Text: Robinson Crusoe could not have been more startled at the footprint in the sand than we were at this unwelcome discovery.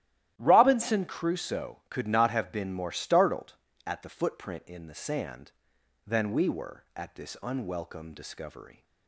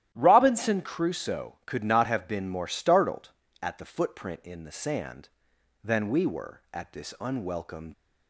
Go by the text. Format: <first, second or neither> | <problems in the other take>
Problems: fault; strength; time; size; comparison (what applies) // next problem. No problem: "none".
first | starts louder than the rest; strong; until 1.1 s; 12.5 dB; strong in the first // stops before "discovery"; at 7.9 s